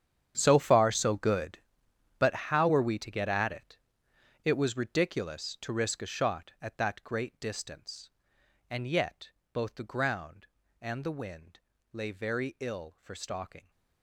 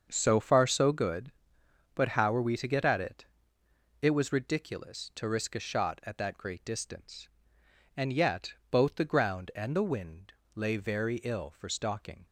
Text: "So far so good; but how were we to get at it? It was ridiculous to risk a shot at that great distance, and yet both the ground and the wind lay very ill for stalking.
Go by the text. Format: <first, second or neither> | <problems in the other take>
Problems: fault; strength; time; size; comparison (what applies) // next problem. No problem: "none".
second | gets quieter; strong; throughout; 16.5 dB // starts louder than the rest; strong; until 1.3 s; 9 dB; also in the second // pauses between "but" and "how"; slight; at 2.3 s; 0.18 s long // pauses between "yet" and "both"; slight; at 9.3 s; 0.22 s long; slight in the second // pauses between "wind" and "lay"; slight; at 11.6 s; 0.32 s long; slight in the second